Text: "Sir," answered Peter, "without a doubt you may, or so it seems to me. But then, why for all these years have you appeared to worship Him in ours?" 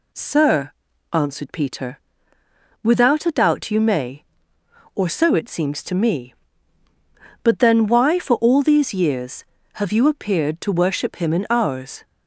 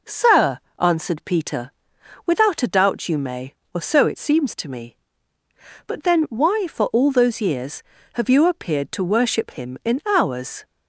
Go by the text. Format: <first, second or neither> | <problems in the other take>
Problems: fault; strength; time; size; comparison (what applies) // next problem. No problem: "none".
first | says "those" for "these"; at 7.1 s